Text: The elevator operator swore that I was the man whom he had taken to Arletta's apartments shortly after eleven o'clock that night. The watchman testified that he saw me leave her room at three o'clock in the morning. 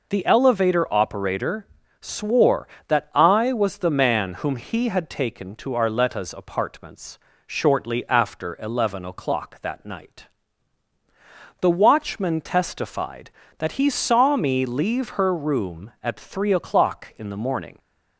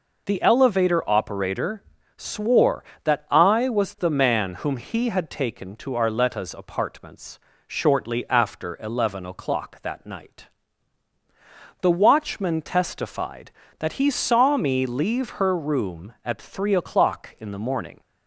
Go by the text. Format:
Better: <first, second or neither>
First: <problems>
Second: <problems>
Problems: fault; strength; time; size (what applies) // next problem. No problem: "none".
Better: neither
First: pauses between "operator" and "swore"; slight; at 1.6 s; 0.34 s long // pauses between "apartments" and "shortly"; slight; at 7.1 s; 0.30 s long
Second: pauses between "operator" and "swore"; slight; at 1.8 s; 0.34 s long // pauses between "apartments" and "shortly"; slight; at 7.3 s; 0.30 s long